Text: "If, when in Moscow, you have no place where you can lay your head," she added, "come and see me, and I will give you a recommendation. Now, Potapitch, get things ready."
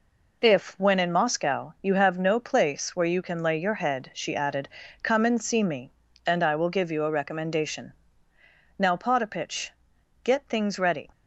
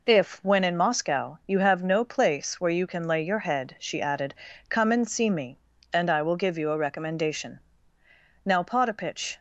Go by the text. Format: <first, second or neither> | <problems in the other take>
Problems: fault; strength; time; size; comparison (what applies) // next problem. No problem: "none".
first | stops before "get things ready"; at 9.3 s